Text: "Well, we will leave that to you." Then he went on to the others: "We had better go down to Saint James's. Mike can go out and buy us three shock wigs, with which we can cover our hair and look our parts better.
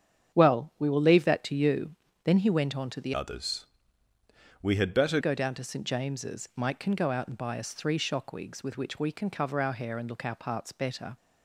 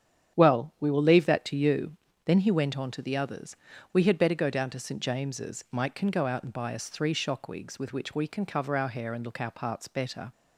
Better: second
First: starts louder than the rest; strong; until 1.3 s; 8.5 dB // changes voice from "others" to "better"; from 3.1 to 5.1 s; 2.0 s long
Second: starts louder than the rest; strong; until 1.4 s; 9 dB

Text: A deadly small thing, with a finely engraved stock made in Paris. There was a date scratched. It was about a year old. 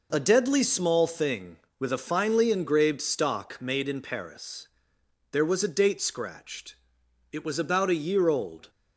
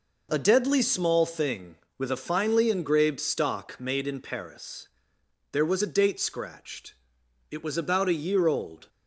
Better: neither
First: none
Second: none

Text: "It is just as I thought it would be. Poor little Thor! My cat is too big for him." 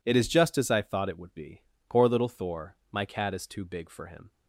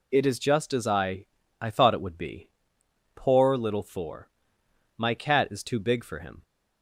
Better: first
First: none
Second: says "I" twice; at 1.6 s

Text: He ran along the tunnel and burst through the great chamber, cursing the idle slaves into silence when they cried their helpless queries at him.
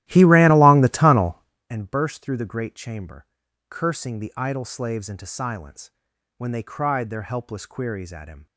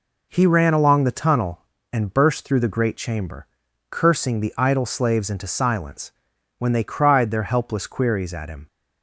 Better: second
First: starts louder than the rest; strong; until 1.7 s; 15 dB // pauses between "silence" and "when"; noticeable; at 5.8 s; 0.48 s long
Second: pauses between "silence" and "when"; noticeable; at 6.1 s; 0.48 s long

